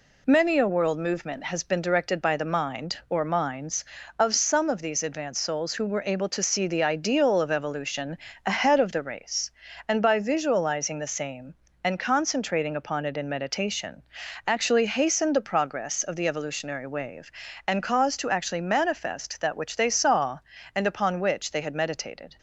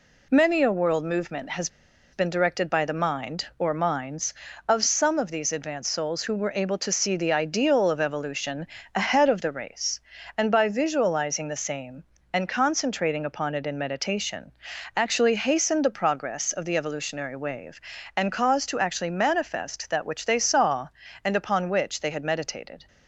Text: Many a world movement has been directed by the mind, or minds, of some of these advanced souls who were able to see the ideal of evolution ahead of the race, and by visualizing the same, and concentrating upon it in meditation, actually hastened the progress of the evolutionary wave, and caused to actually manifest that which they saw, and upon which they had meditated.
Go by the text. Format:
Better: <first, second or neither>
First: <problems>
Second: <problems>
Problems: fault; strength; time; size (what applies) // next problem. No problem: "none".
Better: first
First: pauses between "evolution" and "ahead"; slight; at 8.1 s; 0.26 s long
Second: pauses between "has" and "been"; at 1.6 s; 0.44 s long // pauses between "evolution" and "ahead"; slight; at 8.6 s; 0.26 s long